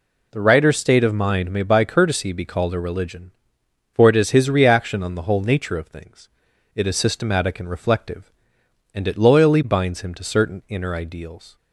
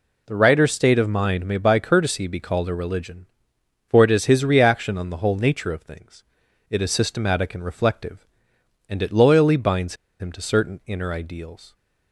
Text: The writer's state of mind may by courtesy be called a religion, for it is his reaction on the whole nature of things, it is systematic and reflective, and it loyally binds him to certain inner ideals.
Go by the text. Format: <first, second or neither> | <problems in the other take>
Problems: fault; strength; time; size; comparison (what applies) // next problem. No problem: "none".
first | pauses between "binds" and "him"; slight; at 9.9 s; 0.24 s long